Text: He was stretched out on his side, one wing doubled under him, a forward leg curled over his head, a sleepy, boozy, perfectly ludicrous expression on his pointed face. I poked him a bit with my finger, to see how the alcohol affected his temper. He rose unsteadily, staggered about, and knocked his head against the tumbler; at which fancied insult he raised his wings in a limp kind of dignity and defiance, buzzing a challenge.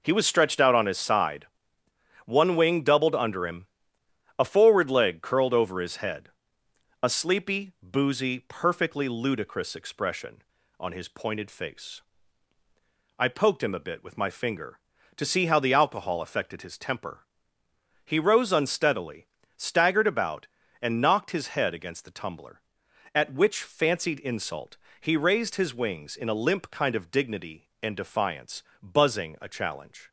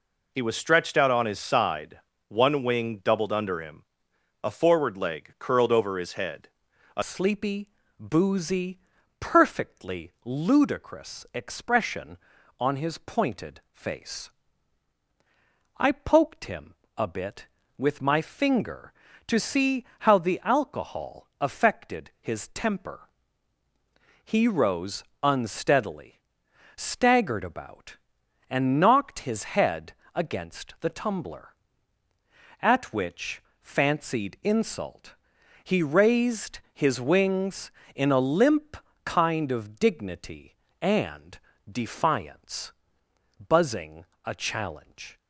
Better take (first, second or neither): first